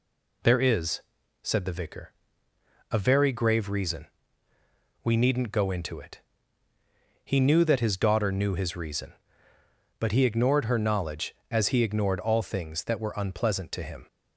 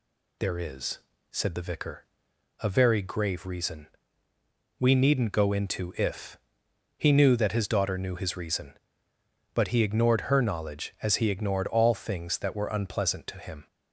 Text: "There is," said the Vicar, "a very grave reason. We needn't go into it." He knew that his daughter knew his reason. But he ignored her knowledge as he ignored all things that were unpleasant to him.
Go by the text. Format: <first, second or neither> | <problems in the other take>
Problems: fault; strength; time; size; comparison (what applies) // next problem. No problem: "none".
first | says "if" for "it"; at 5.9 s